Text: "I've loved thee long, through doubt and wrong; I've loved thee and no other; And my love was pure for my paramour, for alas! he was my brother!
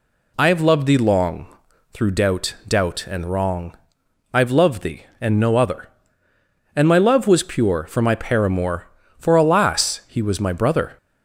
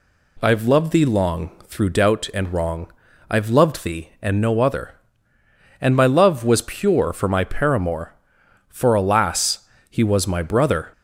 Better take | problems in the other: second | says "doubt" twice; at 2.6 s

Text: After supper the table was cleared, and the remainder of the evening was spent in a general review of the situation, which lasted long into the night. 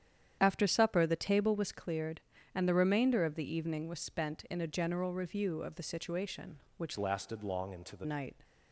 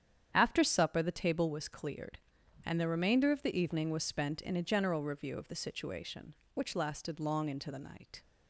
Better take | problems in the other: second | starts louder than the rest; strong; until 1.4 s; 9.5 dB; strong in the second // changes voice from "lasted" to "the"; from 6.9 to 8.0 s; 1.1 s long

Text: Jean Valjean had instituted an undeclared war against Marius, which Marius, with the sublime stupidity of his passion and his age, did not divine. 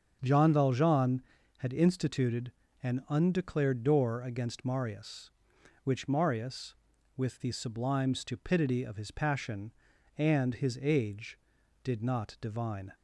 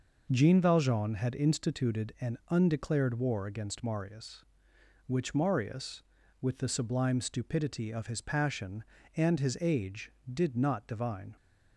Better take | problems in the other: second | starts louder than the rest; until 1.2 s; 7 dB // pauses between "instituted" and "an"; slight; at 2.5 s; 0.32 s long // says "door" for "war"; at 3.8 s

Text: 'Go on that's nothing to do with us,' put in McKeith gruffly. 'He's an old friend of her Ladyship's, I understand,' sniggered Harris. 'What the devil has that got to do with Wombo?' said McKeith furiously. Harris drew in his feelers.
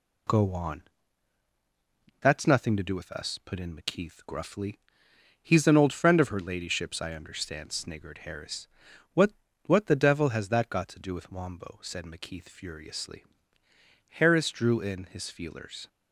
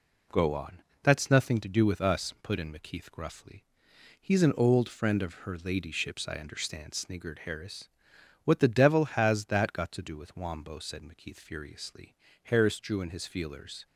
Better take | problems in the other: second | pauses between "on" and "that's"; strong; at 0.8 s; 1.3 s long; slight in the second // says "What" twice; at 9.6 s

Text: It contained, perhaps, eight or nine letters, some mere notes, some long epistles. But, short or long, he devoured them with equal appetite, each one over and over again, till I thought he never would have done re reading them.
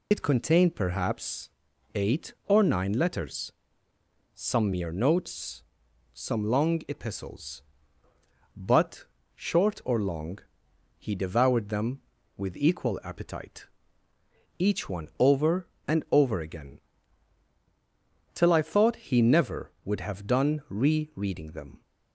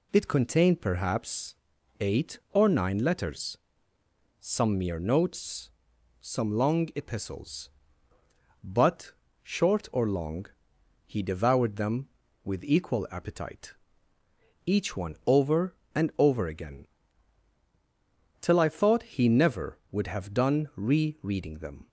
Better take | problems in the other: second | loses the start of "It"; at 0.1 s; 55 ms

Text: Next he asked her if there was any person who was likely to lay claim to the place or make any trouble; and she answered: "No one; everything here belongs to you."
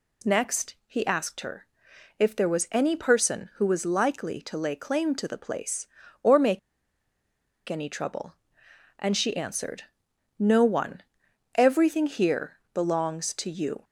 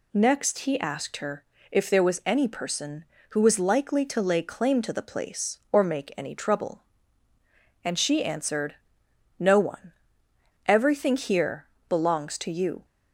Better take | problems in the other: second | pauses between "her" and "if"; noticeable; at 1.6 s; 0.52 s long; slight in the second // pauses between "make" and "any"; at 6.5 s; 1.1 s long // pauses between "here" and "belongs"; slight; at 12.5 s; 0.16 s long; slight in the second

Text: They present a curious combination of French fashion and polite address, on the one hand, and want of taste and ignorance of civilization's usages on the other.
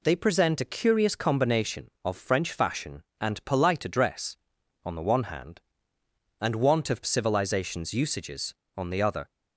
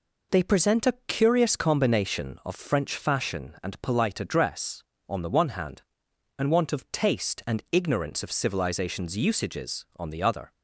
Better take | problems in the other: second | skips "taste and ignorance of"; at 7.0 s

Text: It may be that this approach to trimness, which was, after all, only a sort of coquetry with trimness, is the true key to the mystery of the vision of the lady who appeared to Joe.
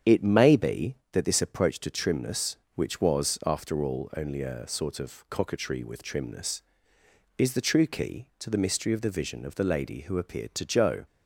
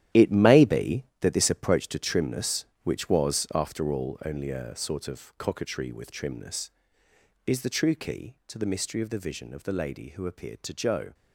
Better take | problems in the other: first | gets quieter; strong; throughout; 12 dB // starts louder than the rest; strong; until 1.3 s; 12 dB; strong in the first

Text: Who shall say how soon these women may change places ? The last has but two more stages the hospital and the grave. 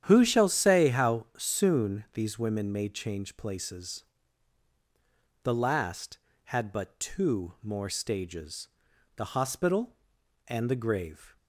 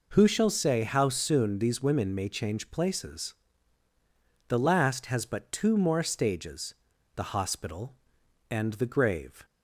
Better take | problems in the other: second | starts louder than the rest; strong; until 1.0 s; 9.5 dB // says "had" for "has"; at 6.4 s // pauses between "stages" and "the"; noticeable; at 8.6 s; 0.48 s long; also in the second

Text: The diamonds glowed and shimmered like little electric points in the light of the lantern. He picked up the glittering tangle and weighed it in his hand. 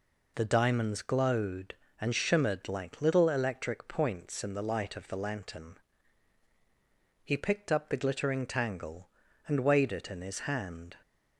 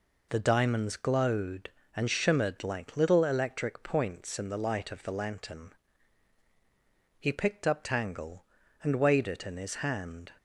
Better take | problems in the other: first | skips "the glittering"; at 7.8 s

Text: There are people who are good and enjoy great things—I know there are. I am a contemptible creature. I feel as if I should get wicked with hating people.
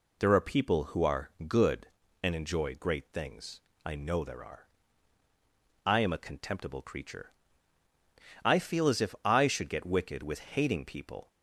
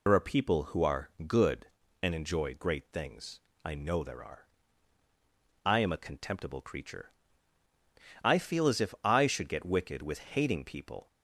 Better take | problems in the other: first | loses the start of "There"; at 0.0 s; 70 ms // pauses between "are" and "good"; slight; at 1.0 s; 0.16 s long; slight in the first

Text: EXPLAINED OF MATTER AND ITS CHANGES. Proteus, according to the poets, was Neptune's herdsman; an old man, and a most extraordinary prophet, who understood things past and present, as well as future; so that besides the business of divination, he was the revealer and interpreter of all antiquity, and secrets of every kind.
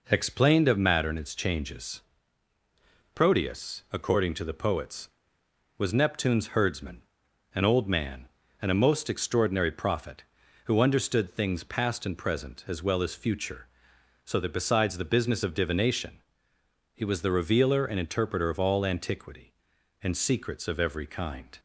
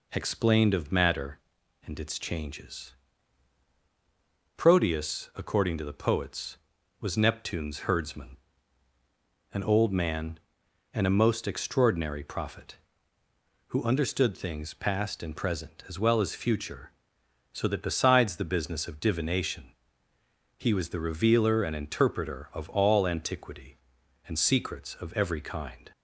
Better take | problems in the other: neither | none

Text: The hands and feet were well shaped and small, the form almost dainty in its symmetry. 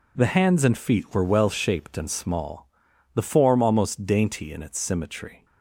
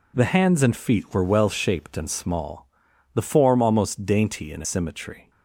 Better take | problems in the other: first | skips "its"; at 4.6 s

